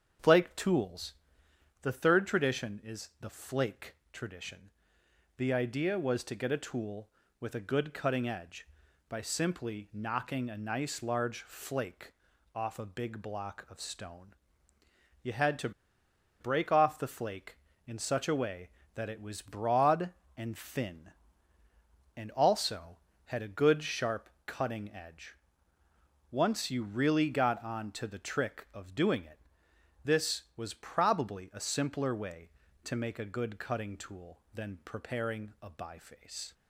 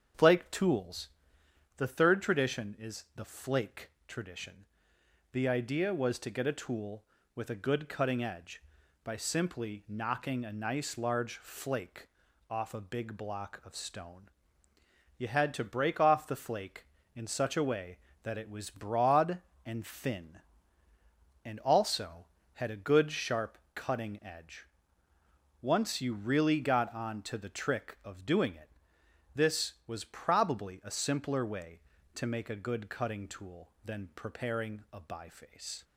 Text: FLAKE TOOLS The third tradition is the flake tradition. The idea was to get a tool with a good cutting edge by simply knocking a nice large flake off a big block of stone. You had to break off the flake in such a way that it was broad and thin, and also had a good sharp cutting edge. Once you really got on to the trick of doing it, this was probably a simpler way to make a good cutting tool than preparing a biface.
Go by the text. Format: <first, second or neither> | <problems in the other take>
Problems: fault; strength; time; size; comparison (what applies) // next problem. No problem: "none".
second | starts louder than the rest; strong; until 1.8 s; 7.5 dB; strong in the second // pauses between "TOOLS" and "The"; noticeable; at 1.1 s; 0.66 s long; noticeable in the second // pauses between "flake" and "tradition"; slight; at 3.9 s; 0.18 s long; slight in the second // pauses between "flake" and "off"; at 12.1 s; 0.42 s long; also in the second // pauses between "to" and "break"; noticeable; at 15.7 s; 0.69 s long // pauses between "sharp" and "cutting"; slight; at 24.2 s; 0.16 s long; slight in the second